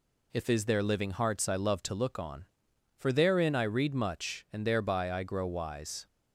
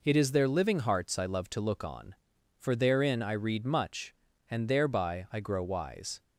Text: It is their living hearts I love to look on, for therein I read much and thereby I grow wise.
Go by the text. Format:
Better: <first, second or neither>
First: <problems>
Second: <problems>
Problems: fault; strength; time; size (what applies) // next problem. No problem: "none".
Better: second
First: says "If" for "It"; at 0.3 s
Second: none